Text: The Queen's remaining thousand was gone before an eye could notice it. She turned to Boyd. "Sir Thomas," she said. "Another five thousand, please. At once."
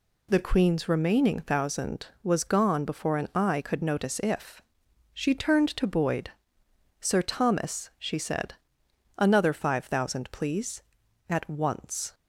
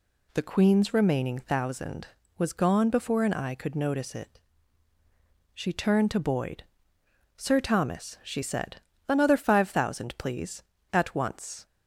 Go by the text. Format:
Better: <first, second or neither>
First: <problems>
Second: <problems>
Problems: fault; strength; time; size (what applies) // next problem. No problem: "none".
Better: second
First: says "if" for "it"; at 4.2 s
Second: none